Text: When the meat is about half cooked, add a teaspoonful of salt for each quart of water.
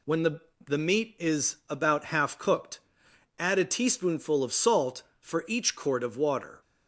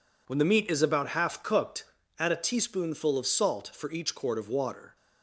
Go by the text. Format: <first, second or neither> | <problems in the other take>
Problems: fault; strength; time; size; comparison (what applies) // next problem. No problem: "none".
second | says "the" twice; at 0.6 s